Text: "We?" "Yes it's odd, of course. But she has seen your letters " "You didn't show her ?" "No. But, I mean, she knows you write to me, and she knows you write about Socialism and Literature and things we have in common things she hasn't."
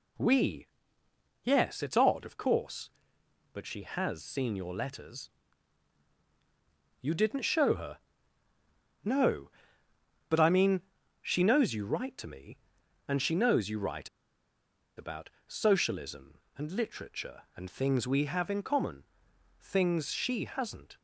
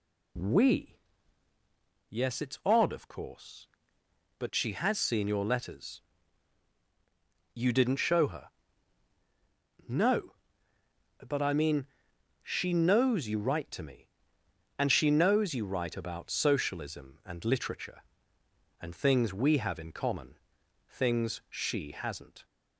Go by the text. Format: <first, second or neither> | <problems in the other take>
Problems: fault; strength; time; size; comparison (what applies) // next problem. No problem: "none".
second | pauses between "write" and "about"; noticeable; at 14.0 s; 0.88 s long // pauses between "about" and "Socialism"; slight; at 15.2 s; 0.18 s long // pauses between "common" and "things"; noticeable; at 19.0 s; 0.56 s long; noticeable in the second